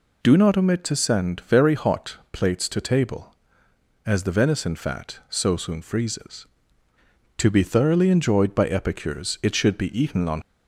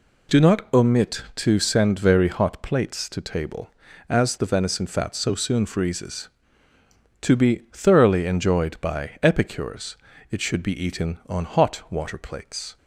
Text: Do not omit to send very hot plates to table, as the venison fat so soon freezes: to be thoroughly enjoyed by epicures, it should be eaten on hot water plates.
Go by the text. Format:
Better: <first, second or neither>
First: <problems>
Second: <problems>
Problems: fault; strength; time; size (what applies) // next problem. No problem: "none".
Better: second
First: stops before "hot water plates"; at 10.4 s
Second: none